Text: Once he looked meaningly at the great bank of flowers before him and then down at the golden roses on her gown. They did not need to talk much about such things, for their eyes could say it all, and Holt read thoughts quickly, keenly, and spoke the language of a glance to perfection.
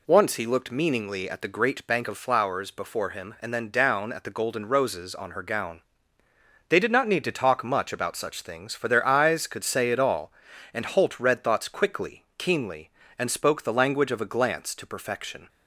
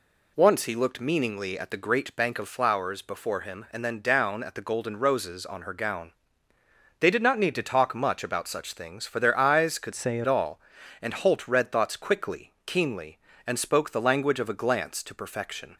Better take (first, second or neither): first